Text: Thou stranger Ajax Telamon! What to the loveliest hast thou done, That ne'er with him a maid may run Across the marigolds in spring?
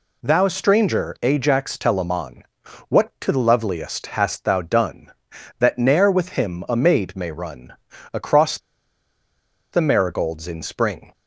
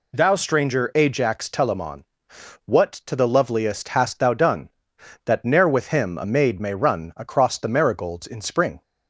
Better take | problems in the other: second | pauses between "run" and "Across"; at 7.7 s; 0.38 s long // pauses between "Across" and "the"; at 8.5 s; 1.1 s long

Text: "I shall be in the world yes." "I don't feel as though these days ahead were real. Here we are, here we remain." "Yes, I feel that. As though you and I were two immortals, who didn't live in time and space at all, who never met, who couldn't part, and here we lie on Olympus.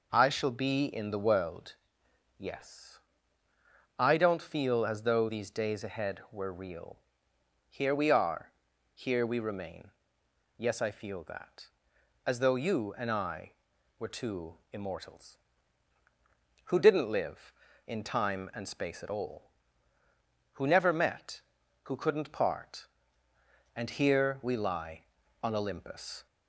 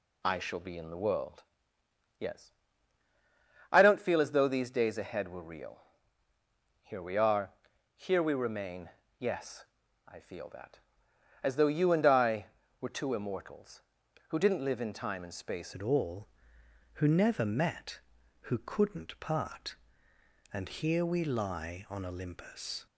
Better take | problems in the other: first | pauses between "world" and "yes"; noticeable; at 1.4 s; 0.74 s long; noticeable in the first // changes voice at "at"; from 15.7 s on; 7.1 s long

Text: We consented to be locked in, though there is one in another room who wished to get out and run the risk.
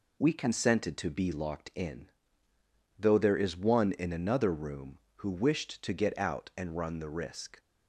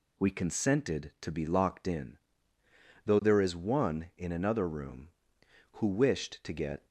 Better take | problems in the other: first | stops before "out and run the risk"; at 6.8 s

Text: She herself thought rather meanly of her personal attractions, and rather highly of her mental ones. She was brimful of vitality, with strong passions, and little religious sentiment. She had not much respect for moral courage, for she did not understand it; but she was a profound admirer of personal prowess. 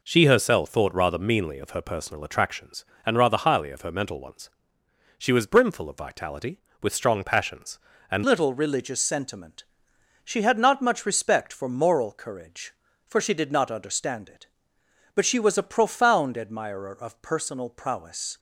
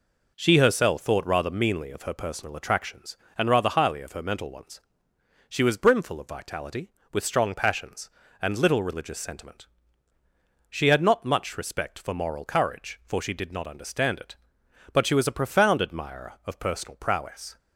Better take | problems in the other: second | changes voice at "little"; from 8.2 s on; 10.1 s long

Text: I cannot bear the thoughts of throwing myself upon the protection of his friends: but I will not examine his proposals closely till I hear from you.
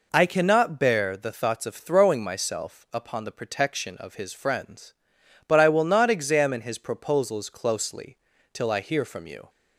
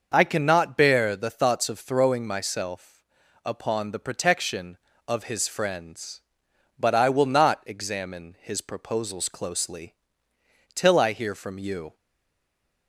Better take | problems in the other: first | starts louder than the rest; noticeable; until 1.1 s; 6 dB // pauses between "myself" and "upon"; noticeable; at 3.0 s; 0.46 s long // pauses between "closely" and "till"; noticeable; at 9.9 s; 0.80 s long; slight in the first // stays silent after the last word; from 11.9 s on; 0.9 s long

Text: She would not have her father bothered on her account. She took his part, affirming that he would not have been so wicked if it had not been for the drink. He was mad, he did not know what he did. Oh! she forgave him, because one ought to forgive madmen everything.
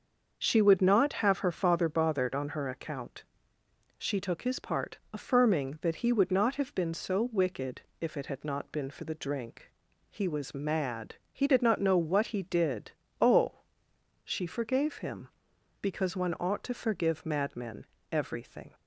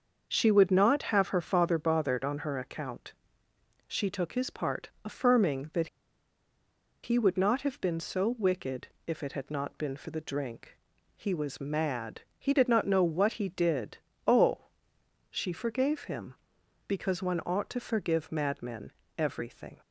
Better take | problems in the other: first | starts louder than the rest; until 1.3 s; 6.5 dB; also in the first // pauses between "that" and "he"; at 5.8 s; 1.1 s long // pauses between "wicked" and "if"; slight; at 8.8 s; 0.20 s long; slight in the first // pauses between "madmen" and "everything"; slight; at 18.9 s; 0.26 s long; slight in the first

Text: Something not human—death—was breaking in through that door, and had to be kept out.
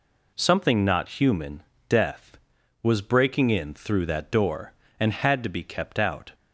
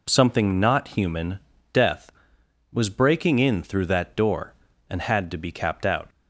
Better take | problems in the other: first | says "capped" for "kept"; at 5.5 s

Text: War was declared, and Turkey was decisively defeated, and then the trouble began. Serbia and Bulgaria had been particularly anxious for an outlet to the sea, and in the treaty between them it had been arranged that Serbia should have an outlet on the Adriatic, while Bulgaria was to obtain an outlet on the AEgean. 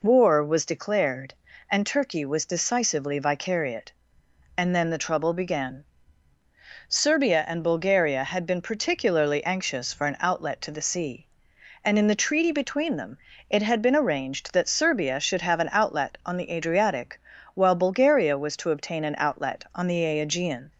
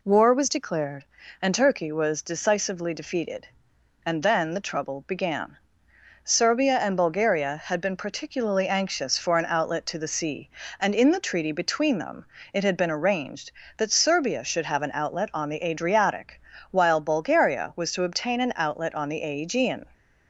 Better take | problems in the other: second | says "vicariate" for "defeated"; at 3.1 s // pauses between "them" and "it"; slight; at 13.1 s; 0.32 s long; slight in the second

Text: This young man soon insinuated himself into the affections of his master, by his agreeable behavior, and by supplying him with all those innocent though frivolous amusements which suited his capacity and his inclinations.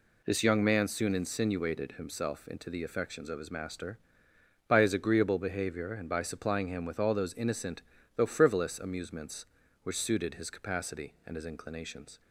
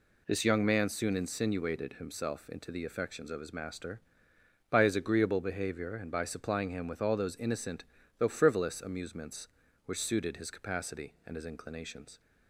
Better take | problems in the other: neither | pauses between "innocent" and "though"; slight; the same in both

